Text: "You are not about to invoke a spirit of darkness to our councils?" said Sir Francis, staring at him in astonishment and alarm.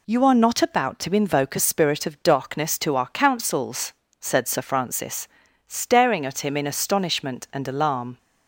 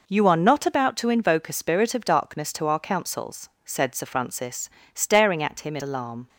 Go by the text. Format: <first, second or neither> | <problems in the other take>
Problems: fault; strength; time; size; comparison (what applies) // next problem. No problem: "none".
first | skips "astonishment and"; at 5.8 s